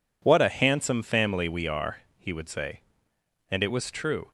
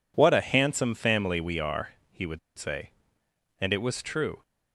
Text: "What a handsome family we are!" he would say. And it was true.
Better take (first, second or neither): first